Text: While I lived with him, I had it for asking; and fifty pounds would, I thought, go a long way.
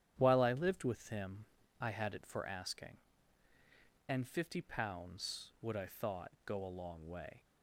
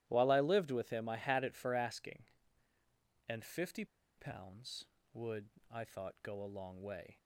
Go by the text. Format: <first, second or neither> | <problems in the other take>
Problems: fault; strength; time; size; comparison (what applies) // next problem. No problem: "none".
first | starts louder than the rest; strong; until 1.0 s; 13.5 dB; strong in the first // pauses between "fifty" and "pounds"; slight; at 3.8 s; 0.33 s long